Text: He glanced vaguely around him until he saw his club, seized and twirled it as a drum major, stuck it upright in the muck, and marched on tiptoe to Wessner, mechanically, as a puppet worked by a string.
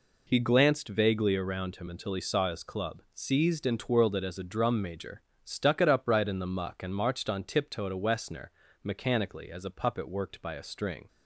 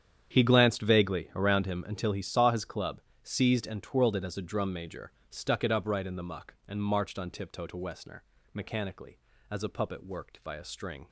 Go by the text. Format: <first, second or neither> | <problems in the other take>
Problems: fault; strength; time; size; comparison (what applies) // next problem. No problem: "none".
first | gets quieter; strong; throughout; 15 dB